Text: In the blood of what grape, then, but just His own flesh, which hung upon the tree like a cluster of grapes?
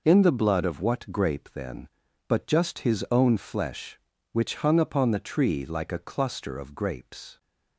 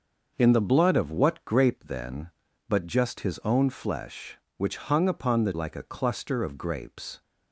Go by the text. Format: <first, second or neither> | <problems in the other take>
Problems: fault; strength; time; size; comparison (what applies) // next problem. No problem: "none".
first | starts louder than the rest; noticeable; until 1.3 s; 6 dB // skips "tree"; at 5.5 s